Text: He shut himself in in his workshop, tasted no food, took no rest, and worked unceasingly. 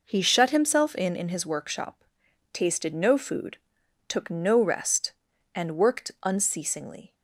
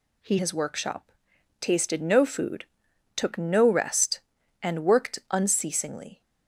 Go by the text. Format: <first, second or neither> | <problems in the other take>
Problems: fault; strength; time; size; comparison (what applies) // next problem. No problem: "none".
first | skips "shut himself in in"; at 0.3 s